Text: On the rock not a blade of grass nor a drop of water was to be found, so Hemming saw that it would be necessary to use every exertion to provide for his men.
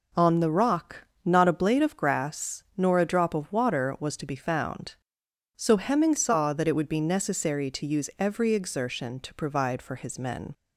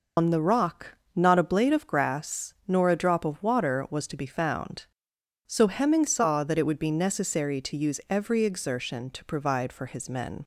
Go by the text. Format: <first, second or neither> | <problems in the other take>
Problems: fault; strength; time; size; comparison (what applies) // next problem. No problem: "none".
first | loses the start of "On"; at 0.1 s; 125 ms // pauses between "rock" and "not"; slight; at 0.9 s; 0.20 s long; slight in the first